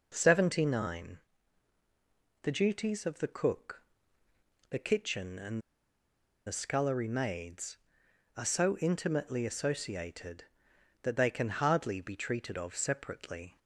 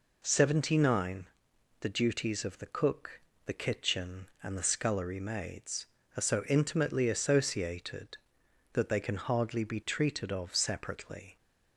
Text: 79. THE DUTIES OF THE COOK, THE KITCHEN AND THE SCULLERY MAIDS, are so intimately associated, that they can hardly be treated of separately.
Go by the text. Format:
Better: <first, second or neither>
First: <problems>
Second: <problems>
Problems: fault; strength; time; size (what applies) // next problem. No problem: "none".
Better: second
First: pauses between "AND" and "THE"; noticeable; at 5.5 s; 0.87 s long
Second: none